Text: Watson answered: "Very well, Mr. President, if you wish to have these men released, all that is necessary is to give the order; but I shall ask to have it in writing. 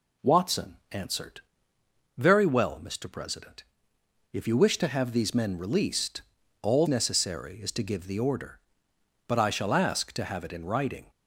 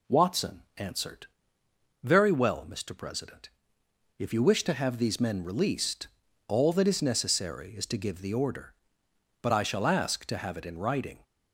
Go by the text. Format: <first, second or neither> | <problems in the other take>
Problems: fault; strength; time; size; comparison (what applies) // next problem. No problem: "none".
second | skips "that is"; at 6.8 s